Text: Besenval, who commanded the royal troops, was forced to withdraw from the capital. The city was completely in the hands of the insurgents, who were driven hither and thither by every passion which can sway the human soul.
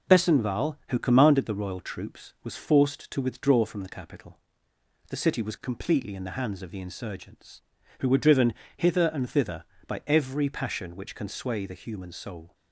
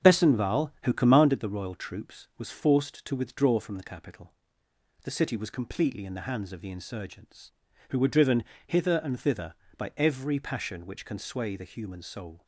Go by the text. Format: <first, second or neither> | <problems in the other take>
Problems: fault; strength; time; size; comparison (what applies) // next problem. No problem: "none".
first | starts louder than the rest; strong; until 1.4 s; 8.5 dB // pauses between "driven" and "hither"; slight; at 8.4 s; 0.24 s long; slight in the first